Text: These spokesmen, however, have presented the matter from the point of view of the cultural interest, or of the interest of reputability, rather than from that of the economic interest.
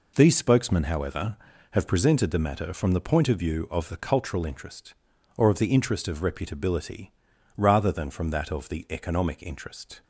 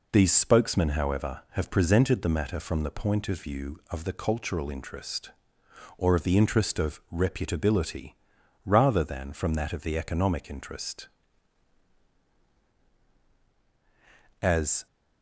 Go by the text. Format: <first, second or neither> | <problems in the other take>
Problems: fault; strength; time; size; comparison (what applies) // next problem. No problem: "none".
first | goes on to say "As"; slight; from 14.4 s on; 0.46 s long